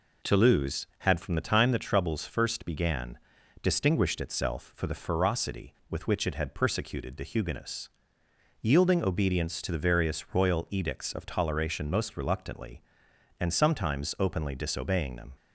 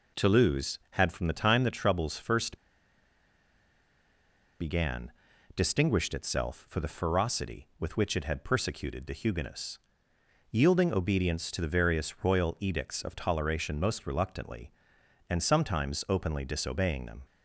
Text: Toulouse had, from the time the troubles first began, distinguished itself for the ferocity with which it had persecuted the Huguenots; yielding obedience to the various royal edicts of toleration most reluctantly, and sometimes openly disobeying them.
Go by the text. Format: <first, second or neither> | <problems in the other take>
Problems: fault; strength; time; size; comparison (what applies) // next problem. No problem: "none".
first | pauses between "first" and "began"; strong; at 2.5 s; 2.0 s long